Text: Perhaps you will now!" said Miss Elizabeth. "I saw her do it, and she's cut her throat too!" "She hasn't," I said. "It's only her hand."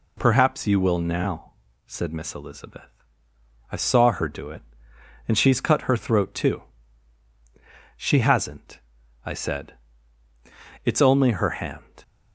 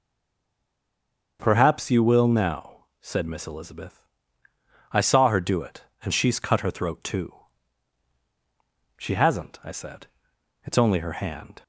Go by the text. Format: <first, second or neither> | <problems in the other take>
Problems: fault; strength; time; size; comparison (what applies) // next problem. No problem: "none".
first | stays silent before the first word; noticeable; until 1.3 s; 1.3 s long // starts louder than the rest; until 2.4 s; 6 dB